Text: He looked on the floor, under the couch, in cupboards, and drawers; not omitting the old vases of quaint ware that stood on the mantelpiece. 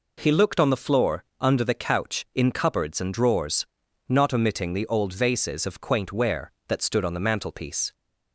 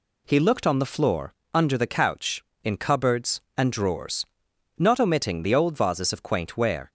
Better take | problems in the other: first | stops before "that stood on the mantelpiece"; at 6.8 s

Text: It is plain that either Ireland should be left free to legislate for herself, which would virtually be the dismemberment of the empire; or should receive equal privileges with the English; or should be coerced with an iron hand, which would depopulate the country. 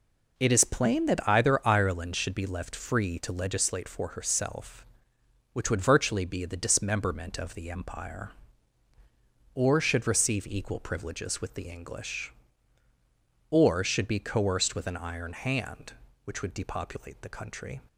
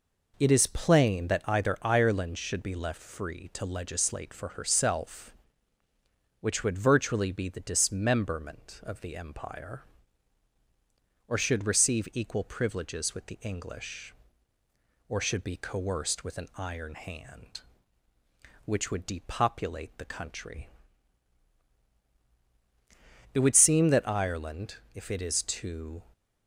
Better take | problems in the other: first | goes on to say "It would seem that Ireland if it is to"; strong; from 23.3 s on; 2.7 s long

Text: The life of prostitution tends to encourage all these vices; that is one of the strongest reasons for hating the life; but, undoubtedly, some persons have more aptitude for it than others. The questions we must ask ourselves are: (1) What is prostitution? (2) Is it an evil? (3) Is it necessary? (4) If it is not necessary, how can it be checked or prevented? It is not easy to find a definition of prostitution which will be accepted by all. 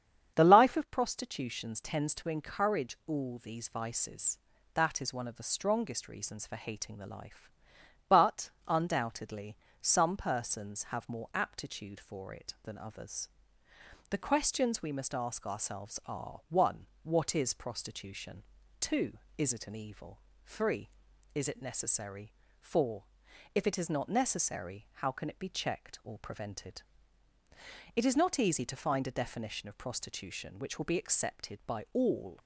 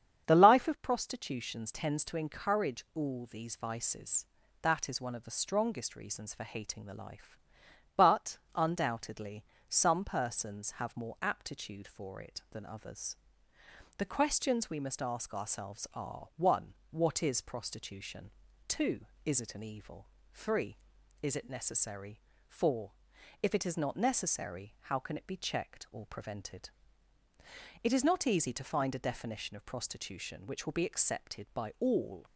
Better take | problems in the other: neither | starts louder than the rest; strong; the same in both

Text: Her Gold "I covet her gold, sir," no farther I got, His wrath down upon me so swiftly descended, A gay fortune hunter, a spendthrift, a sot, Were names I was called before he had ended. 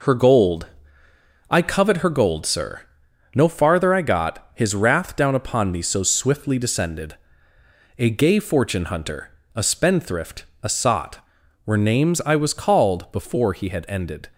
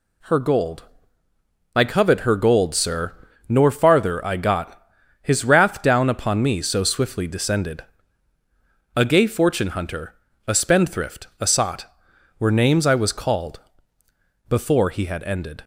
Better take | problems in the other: first | pauses between "Gold" and "I"; noticeable; at 0.8 s; 0.90 s long; noticeable in the first // says "nor" for "no"; at 3.4 s // pauses between "called" and "before"; noticeable; at 13.6 s; 0.86 s long

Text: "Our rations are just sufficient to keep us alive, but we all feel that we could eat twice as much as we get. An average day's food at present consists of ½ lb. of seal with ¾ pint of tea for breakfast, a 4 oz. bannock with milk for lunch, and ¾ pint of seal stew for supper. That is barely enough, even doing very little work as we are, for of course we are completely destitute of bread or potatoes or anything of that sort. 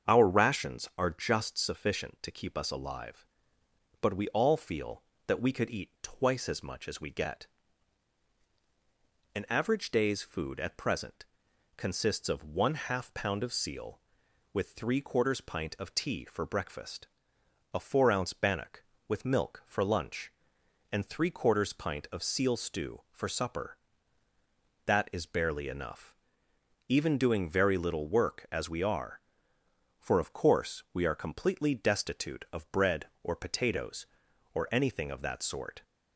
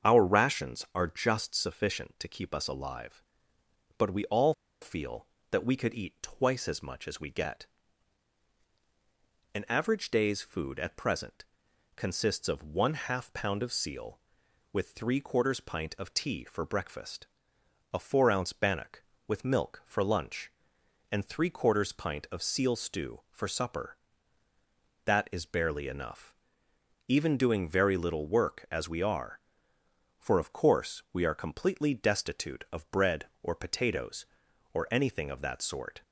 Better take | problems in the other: first | starts louder than the rest; strong; until 1.1 s; 7 dB; also in the first // pauses between "all" and "feel"; slight; at 4.5 s; 0.28 s long // pauses between "present" and "consists"; noticeable; at 11.4 s; 0.52 s long; noticeable in the first

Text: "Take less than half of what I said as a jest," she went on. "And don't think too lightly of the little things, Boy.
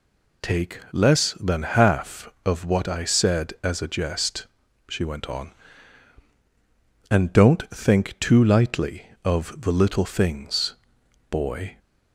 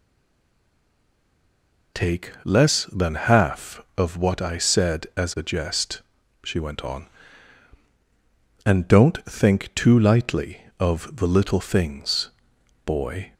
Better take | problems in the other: first | stays silent before the first word; noticeable; until 1.9 s; 1.9 s long

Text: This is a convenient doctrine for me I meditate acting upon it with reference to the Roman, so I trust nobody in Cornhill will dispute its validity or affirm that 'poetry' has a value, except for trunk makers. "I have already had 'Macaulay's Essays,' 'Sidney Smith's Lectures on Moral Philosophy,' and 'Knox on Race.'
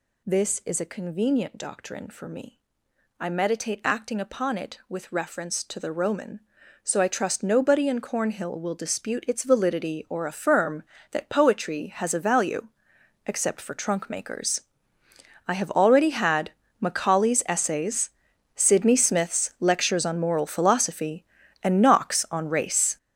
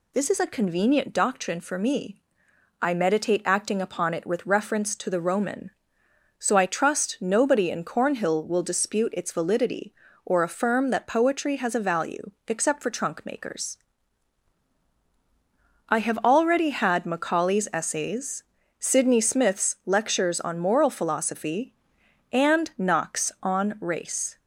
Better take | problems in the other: second | gets louder; strong; throughout; 11 dB // pauses between "me" and "I"; noticeable; at 2.5 s; 0.60 s long; noticeable in the second // pauses between "had" and "Macaulay's"; slight; at 16.5 s; 0.30 s long

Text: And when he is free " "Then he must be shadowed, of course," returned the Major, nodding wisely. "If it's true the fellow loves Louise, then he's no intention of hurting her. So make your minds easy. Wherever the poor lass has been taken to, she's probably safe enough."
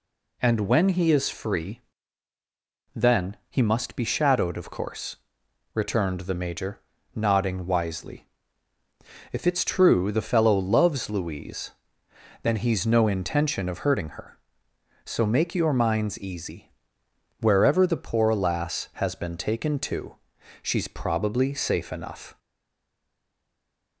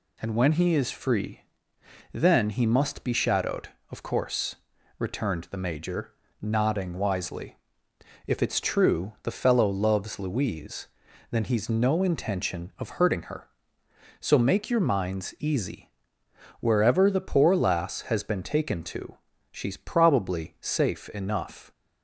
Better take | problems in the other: second | stays silent after the last word; noticeable; from 22.3 s on; 1.7 s long

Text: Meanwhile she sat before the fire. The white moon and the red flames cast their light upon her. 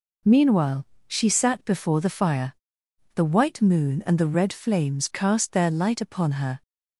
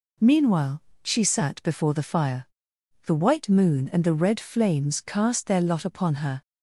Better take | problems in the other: first | pauses between "Meanwhile" and "she"; slight; at 0.8 s; 0.22 s long; slight in the first // says "lot" for "light"; at 5.6 s

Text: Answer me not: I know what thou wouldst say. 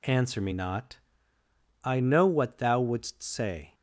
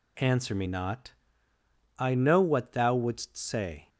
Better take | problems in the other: neither | none

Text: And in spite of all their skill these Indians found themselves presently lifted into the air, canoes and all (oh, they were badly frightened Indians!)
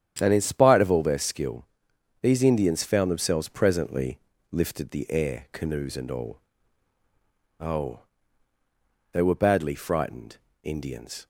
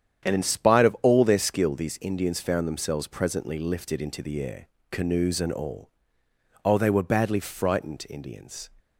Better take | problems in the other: second | starts louder than the rest; strong; until 1.2 s; 9.5 dB; strong in the second // pauses between "skill" and "these"; noticeable; at 1.6 s; 0.58 s long // pauses between "presently" and "lifted"; slight; at 4.1 s; 0.34 s long // skips "into"; at 4.8 s // pauses between "frightened" and "Indians"; slight; at 10.3 s; 0.26 s long

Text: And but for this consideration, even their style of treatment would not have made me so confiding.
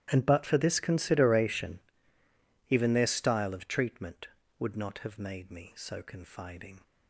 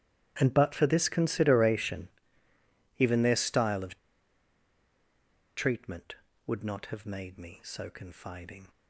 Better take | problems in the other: first | starts louder than the rest; strong; until 1.3 s; 13 dB; strong in the first // pauses between "of" and "treatment"; strong; at 3.9 s; 1.5 s long

